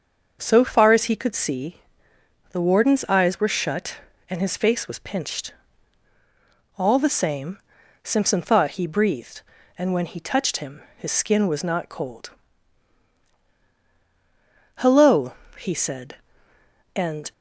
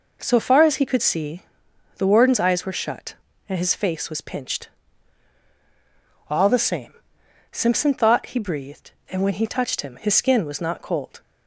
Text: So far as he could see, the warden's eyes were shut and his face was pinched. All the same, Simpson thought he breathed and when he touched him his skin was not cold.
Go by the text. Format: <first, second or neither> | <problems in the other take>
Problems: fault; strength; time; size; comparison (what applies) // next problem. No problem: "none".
second | starts louder than the rest; until 1.4 s; 6 dB // pauses between "him" and "his"; slight; at 10.7 s; 0.16 s long // goes on to say "Hello he said and"; strong; from 14.7 s on; 2.5 s long